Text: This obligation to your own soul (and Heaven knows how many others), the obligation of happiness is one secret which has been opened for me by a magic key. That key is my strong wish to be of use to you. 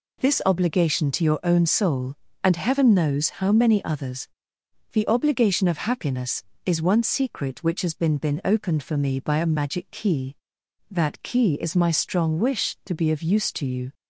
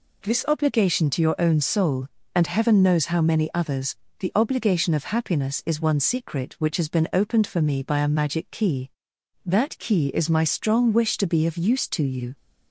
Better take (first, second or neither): second